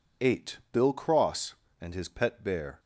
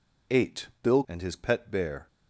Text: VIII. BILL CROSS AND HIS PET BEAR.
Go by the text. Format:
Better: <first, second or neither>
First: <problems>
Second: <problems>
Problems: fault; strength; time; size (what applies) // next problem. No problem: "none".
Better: first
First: none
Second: skips "CROSS"; at 1.0 s